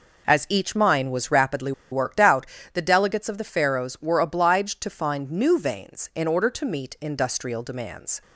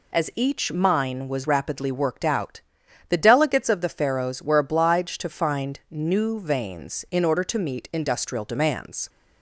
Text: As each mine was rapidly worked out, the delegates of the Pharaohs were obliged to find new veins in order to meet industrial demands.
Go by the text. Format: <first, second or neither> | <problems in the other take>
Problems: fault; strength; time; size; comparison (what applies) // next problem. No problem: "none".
second | pauses between "rapidly" and "worked"; slight; at 1.7 s; 0.19 s long